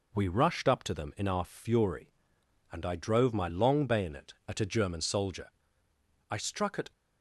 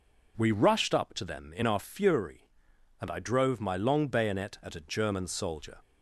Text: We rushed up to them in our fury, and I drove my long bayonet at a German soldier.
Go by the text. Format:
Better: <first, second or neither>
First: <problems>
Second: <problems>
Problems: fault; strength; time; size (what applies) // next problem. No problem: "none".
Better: second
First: goes on to say "I struck at"; noticeable; from 6.2 s on; 0.62 s long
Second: none